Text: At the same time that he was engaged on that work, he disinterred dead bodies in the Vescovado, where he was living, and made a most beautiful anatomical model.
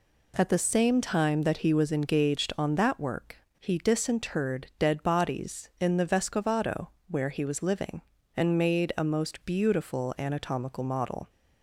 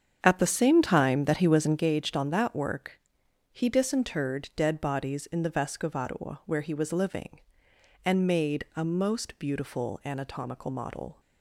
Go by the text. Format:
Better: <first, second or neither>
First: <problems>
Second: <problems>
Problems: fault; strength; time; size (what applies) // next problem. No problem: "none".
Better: first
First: none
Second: starts louder than the rest; strong; until 1.9 s; 7.5 dB